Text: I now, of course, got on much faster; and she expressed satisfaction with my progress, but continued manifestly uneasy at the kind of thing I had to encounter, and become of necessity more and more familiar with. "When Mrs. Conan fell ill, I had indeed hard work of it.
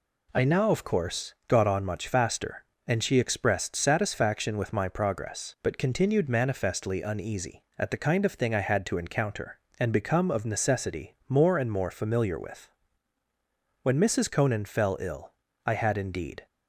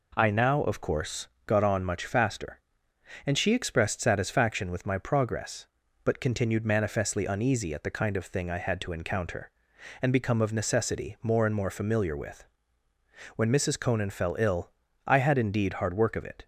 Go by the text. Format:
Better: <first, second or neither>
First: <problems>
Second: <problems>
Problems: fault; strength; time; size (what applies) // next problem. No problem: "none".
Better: second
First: stops before "hard work of it"; at 16.4 s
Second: none